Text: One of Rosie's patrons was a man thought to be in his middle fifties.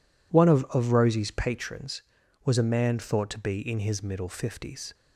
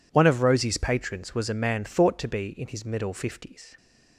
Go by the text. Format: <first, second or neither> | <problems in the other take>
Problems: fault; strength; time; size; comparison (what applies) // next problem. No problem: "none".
second | says "of" twice; at 0.6 s